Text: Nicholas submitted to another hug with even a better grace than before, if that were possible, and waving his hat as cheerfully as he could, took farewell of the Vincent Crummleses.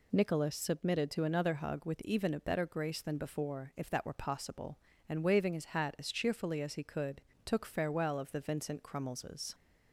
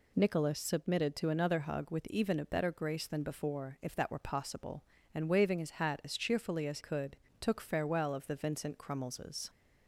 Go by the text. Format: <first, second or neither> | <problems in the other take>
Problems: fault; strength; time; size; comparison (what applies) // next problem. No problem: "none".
first | skips "he"; at 6.7 s